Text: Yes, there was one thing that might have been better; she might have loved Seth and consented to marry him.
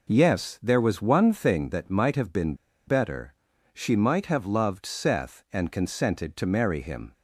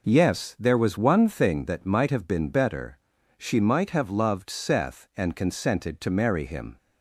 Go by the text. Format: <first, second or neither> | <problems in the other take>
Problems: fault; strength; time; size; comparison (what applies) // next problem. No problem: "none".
second | pauses between "been" and "better"; slight; at 2.5 s; 0.32 s long